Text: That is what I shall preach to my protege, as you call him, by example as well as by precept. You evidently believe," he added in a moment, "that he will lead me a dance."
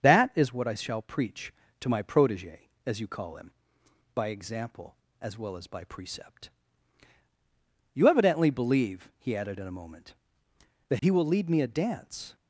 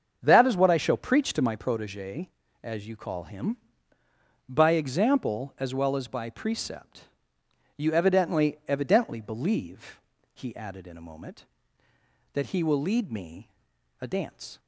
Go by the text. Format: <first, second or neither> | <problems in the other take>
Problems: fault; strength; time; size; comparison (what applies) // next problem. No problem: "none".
first | starts louder than the rest; until 1.2 s; 7 dB; also in the first // says "evidently" twice; at 8.6 s // pauses between "me" and "a"; noticeable; at 13.4 s; 0.54 s long